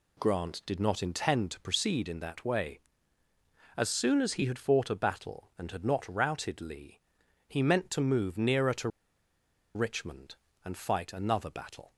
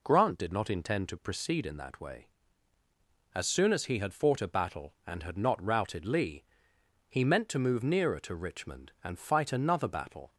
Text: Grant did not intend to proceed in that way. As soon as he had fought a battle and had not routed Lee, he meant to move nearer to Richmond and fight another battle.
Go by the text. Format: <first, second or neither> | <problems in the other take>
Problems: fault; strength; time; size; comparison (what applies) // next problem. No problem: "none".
second | pauses between "to" and "Richmond"; noticeable; at 8.8 s; 0.86 s long